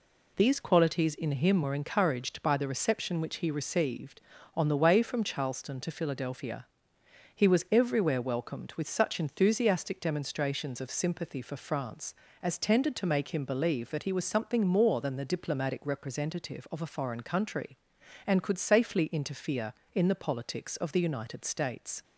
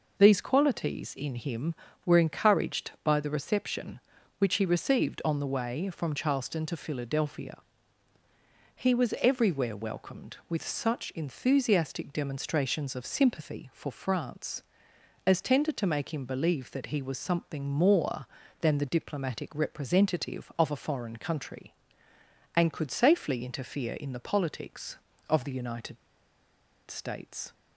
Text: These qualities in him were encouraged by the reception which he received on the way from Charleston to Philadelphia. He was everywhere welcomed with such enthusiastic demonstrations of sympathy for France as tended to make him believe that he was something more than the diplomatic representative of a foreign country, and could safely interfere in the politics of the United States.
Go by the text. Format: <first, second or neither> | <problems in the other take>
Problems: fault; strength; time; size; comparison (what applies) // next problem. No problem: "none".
first | pauses between "United" and "States"; noticeable; at 25.9 s; 0.93 s long